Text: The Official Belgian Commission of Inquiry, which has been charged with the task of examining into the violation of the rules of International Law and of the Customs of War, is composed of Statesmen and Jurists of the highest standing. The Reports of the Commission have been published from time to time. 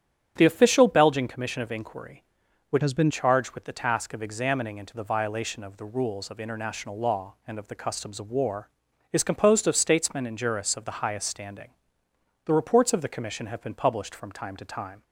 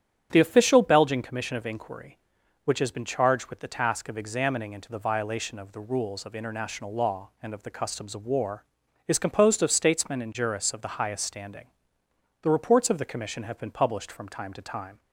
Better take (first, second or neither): second